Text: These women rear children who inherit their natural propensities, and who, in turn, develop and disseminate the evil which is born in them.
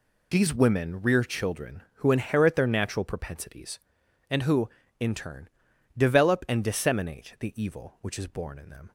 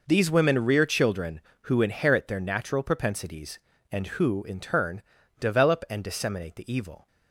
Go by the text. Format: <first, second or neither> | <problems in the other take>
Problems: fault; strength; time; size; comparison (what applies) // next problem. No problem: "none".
first | stops before "which is born in them"; at 7.0 s